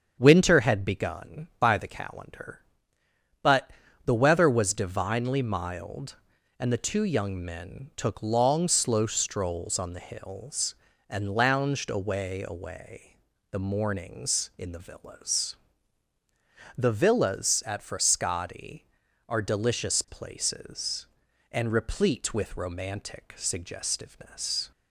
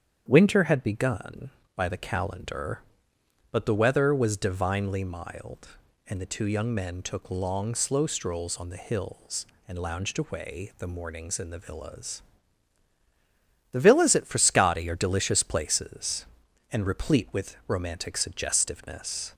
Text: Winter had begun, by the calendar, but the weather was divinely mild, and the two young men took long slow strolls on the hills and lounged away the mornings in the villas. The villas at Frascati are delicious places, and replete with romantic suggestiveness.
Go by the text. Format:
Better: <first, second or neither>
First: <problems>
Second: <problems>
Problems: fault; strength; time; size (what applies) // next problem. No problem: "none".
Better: second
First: starts louder than the rest; strong; until 1.2 s; 7.5 dB // pauses between "but" and "the"; at 3.6 s; 0.38 s long // says "away" twice; at 12.4 s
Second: starts louder than the rest; strong; until 1.2 s; 8.5 dB